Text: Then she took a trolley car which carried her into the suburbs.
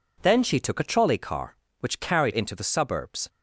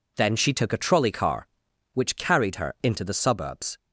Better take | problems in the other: second | skips "her"; at 2.3 s

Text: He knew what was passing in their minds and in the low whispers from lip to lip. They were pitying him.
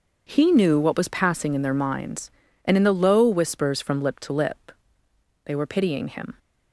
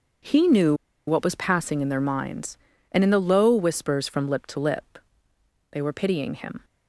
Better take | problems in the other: first | pauses between "knew" and "what"; slight; at 0.7 s; 0.33 s long

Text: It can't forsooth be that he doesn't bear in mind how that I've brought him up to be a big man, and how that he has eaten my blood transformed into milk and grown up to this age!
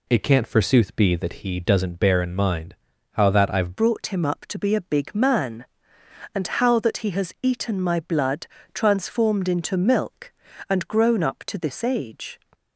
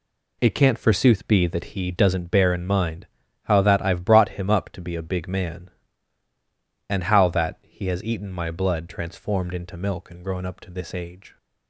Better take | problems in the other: second | pauses between "mind" and "how"; at 2.7 s; 0.38 s long; also in the second // changes voice at "brought"; from 3.7 s on; 8.6 s long // pauses between "blood" and "transformed"; slight; at 8.4 s; 0.26 s long

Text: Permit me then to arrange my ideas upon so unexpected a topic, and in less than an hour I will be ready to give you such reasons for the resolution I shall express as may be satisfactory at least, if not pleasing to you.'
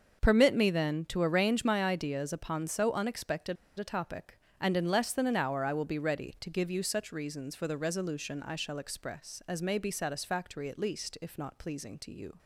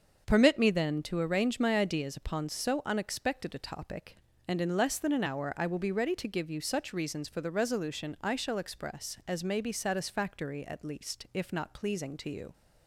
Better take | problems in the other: second | starts louder than the rest; until 1.2 s; 6.5 dB; also in the second // pauses between "unexpected" and "a"; slight; at 3.5 s; 0.22 s long

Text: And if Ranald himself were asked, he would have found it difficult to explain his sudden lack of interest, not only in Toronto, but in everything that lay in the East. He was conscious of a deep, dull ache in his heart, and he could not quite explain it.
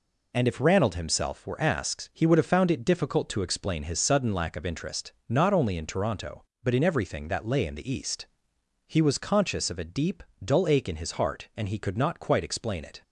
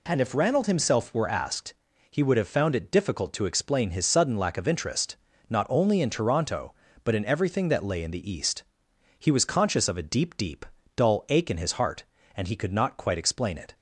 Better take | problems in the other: first | says "deep" twice; at 10.3 s

